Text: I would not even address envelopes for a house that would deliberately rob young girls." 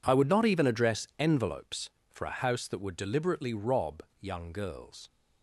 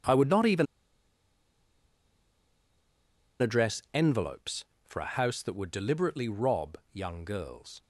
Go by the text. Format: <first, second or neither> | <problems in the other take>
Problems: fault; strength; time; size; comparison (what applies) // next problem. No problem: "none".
first | pauses between "even" and "address"; strong; at 0.6 s; 2.7 s long // pauses between "rob" and "young"; slight; at 6.7 s; 0.16 s long; slight in the first